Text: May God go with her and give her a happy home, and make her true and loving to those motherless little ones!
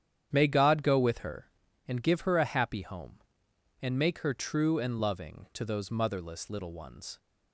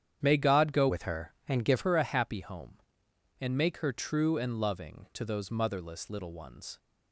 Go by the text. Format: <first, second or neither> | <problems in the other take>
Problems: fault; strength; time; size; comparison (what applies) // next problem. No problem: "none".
first | starts louder than the rest; strong; until 1.2 s; 9 dB; strong in the first // changes voice from "with" to "give"; from 0.8 to 1.8 s; 1.0 s long